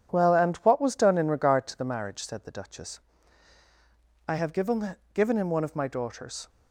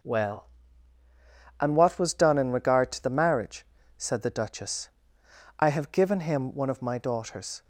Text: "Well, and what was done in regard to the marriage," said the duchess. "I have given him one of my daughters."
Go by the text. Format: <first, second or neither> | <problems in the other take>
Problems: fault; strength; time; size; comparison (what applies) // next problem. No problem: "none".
second | says "given" twice; at 5.1 s